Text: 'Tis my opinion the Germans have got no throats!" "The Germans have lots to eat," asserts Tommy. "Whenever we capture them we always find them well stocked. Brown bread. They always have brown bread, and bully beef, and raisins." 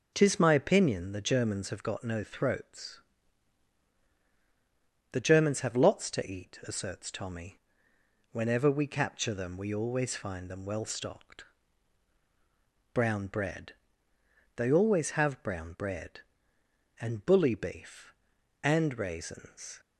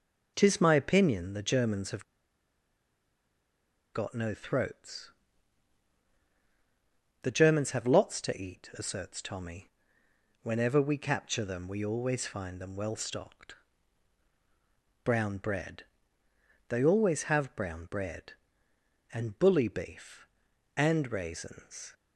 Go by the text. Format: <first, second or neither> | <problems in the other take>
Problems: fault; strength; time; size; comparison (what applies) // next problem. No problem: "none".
first | pauses between "have" and "got"; strong; at 2.0 s; 1.8 s long